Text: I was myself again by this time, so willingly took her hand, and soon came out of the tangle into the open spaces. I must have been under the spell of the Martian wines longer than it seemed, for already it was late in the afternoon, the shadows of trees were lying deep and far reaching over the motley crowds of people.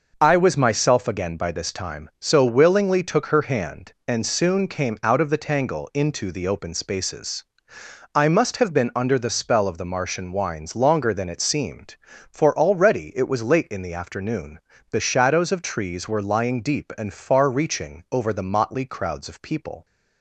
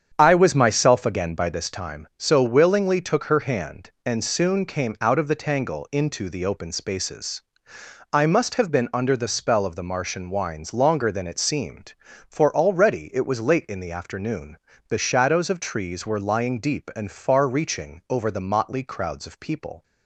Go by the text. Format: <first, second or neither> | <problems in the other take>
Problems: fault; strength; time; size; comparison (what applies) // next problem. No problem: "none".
first | starts louder than the rest; strong; until 1.7 s; 8 dB